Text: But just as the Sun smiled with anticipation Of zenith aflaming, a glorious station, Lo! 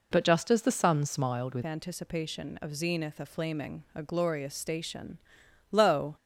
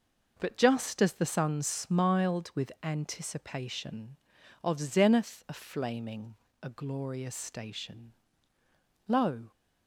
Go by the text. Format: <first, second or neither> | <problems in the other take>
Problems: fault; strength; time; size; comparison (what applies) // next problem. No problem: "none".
second | changes voice at "anticipation"; from 1.6 s on; 4.5 s long